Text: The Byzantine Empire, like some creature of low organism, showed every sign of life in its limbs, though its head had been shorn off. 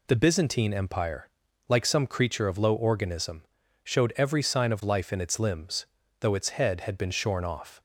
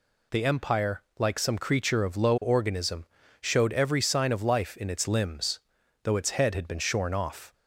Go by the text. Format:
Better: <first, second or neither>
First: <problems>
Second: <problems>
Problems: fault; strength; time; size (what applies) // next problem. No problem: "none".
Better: first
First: none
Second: skips "Byzantine"; at 0.4 s